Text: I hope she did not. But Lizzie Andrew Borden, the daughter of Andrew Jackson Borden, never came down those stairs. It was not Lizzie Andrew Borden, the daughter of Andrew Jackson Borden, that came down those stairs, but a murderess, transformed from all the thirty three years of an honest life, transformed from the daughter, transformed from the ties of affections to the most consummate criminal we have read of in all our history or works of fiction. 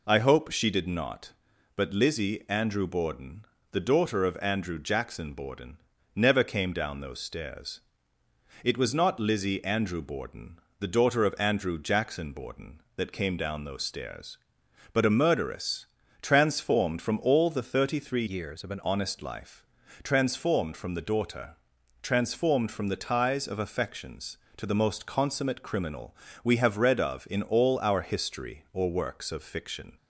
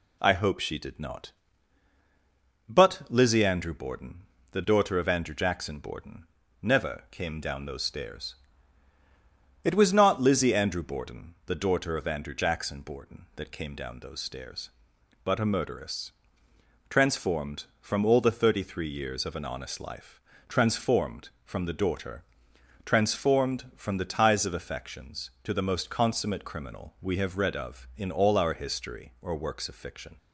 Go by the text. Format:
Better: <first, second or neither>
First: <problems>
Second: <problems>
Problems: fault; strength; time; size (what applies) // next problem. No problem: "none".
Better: second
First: changes voice from "years" to "an"; from 18.2 to 18.8 s; 0.6 s long // pauses between "criminal" and "we"; slight; at 26.1 s; 0.28 s long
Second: none